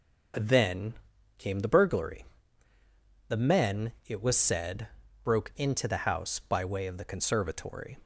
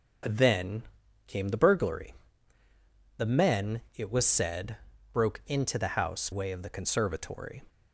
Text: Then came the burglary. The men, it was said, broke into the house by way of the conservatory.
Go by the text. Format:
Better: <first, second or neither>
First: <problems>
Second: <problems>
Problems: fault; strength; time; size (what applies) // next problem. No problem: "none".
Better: first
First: pauses between "Then" and "came"; at 0.9 s; 0.42 s long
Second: pauses between "Then" and "came"; at 0.8 s; 0.42 s long // skips "by"; at 6.3 s